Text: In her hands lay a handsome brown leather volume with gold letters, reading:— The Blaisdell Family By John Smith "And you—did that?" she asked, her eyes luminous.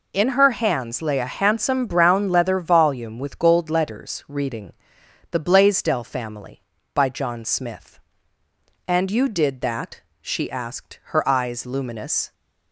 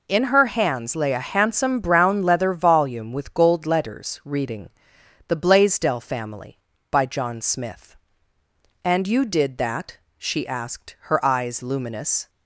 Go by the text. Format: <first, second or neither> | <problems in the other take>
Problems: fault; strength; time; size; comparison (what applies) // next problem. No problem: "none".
neither | none